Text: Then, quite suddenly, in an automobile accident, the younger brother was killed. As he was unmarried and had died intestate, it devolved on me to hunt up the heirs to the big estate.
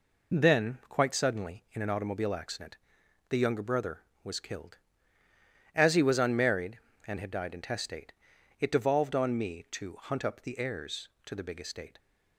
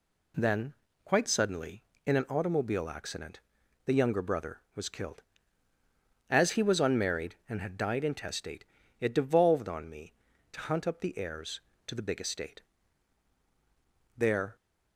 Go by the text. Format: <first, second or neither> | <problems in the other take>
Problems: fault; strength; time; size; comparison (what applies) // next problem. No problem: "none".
first | goes on to say "There"; slight; from 14.1 s on; 0.38 s long